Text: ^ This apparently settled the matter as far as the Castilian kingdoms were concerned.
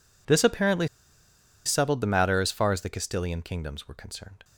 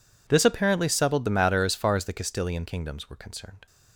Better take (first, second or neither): second